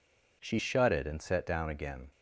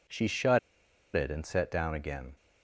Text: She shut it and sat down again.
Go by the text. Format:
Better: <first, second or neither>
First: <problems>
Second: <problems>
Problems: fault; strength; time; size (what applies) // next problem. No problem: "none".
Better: first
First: none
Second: pauses between "shut" and "it"; noticeable; at 0.5 s; 0.56 s long